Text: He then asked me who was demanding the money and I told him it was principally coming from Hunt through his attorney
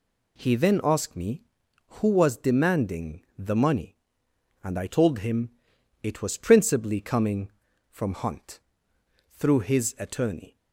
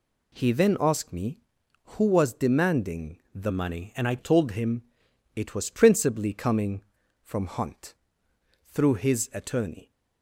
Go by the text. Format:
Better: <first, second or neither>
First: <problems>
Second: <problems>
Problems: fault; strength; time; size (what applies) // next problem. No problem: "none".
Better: first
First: pauses between "demanding" and "the"; slight; at 3.2 s; 0.16 s long // pauses between "him" and "it"; noticeable; at 5.5 s; 0.52 s long // pauses between "Hunt" and "through"; noticeable; at 8.5 s; 0.72 s long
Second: pauses between "demanding" and "the"; slight; at 3.1 s; 0.16 s long // changes voice from "money" to "I"; from 3.5 to 4.1 s; 0.6 s long // pauses between "him" and "it"; noticeable; at 4.8 s; 0.52 s long // pauses between "Hunt" and "through"; noticeable; at 7.9 s; 0.72 s long